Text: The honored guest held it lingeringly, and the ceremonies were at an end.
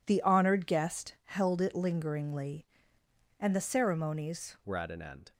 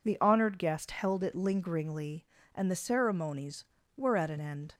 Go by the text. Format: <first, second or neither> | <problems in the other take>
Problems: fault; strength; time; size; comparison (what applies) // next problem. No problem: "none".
second | changes voice at "were"; from 4.6 s on; 0.7 s long